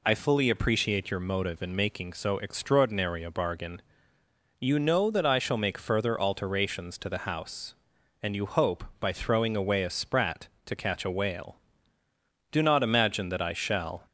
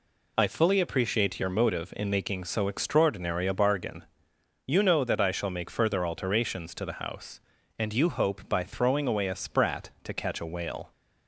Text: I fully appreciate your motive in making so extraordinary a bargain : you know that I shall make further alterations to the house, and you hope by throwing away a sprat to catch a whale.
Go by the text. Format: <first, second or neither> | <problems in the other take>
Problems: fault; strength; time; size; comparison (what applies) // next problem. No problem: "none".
second | goes on to say "Do not imagine that I shall"; from 12.5 s on; 1.5 s long